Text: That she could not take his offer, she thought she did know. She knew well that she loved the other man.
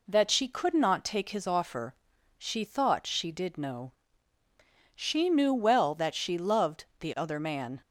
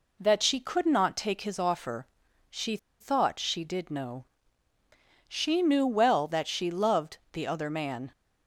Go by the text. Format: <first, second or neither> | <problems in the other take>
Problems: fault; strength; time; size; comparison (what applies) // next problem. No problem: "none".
first | pauses between "she" and "thought"; slight; at 2.7 s; 0.23 s long